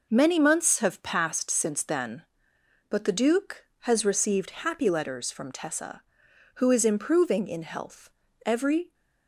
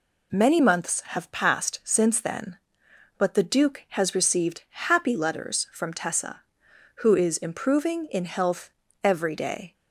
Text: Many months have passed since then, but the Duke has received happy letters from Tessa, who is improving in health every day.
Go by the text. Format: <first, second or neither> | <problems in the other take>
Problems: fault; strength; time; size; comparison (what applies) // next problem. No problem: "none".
second | pauses between "health" and "every"; slight; at 8.0 s; 0.36 s long; slight in the second // stops before "day"; at 8.9 s